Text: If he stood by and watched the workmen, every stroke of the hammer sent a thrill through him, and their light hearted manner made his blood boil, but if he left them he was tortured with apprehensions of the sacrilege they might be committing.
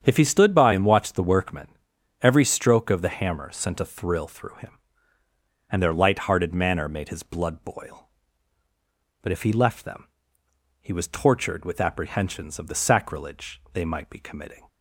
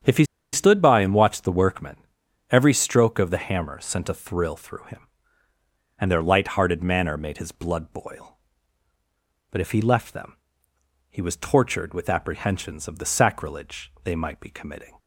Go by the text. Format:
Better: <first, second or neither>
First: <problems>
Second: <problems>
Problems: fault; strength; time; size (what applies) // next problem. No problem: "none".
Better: first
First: starts louder than the rest; strong; until 1.0 s; 8 dB // pauses between "them" and "he"; noticeable; at 10.0 s; 0.76 s long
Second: starts louder than the rest; strong; until 1.3 s; 8 dB // pauses between "he" and "stood"; slight; at 0.2 s; 0.29 s long // pauses between "them" and "he"; noticeable; at 10.3 s; 0.76 s long